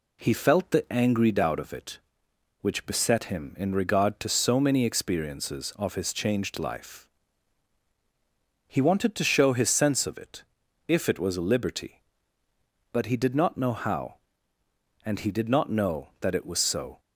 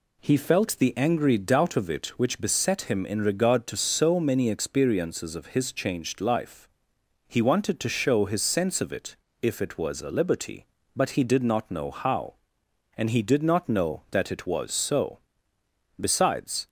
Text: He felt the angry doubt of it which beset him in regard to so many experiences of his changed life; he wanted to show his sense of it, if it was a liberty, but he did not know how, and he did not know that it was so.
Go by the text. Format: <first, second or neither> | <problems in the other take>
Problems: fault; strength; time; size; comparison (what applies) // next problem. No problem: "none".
first | goes on to say "Besides"; noticeable; from 15.9 s on; 0.70 s long